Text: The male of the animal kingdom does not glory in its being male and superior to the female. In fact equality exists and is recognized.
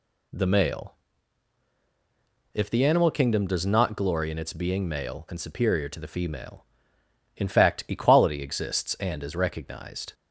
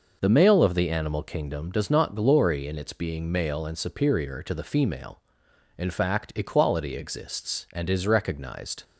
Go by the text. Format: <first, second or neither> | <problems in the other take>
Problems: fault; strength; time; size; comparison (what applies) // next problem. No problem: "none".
second | says "if" for "of"; at 2.5 s